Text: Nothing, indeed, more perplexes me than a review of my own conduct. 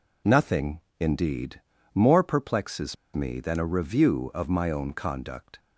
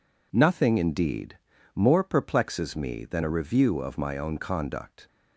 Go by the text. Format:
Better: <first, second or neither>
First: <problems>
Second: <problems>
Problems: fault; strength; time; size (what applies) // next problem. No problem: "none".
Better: second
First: pauses between "perplexes" and "me"; slight; at 2.9 s; 0.19 s long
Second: none